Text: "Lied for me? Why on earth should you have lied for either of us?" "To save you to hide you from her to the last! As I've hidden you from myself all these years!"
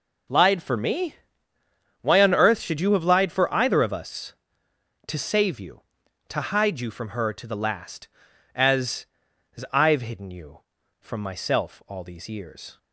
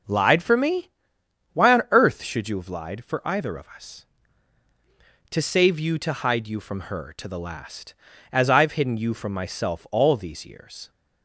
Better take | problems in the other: second | says "As" twice; at 9.5 s

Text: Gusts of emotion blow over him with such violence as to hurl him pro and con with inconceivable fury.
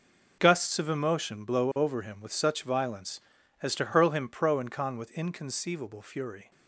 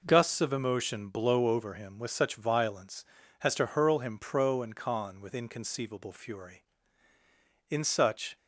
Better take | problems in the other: first | goes on to say "In such"; noticeable; from 7.6 s on; 0.66 s long

